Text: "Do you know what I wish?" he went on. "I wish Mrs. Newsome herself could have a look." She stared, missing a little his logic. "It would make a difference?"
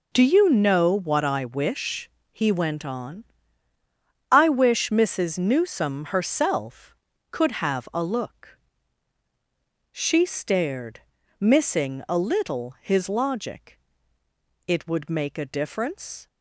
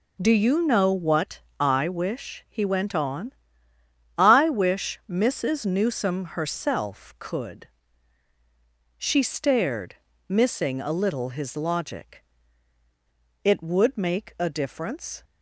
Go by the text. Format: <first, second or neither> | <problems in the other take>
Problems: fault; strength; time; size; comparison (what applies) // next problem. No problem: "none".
first | pauses between "what" and "I"; slight; at 1.4 s; 0.18 s long // skips "have a look"; at 8.3 s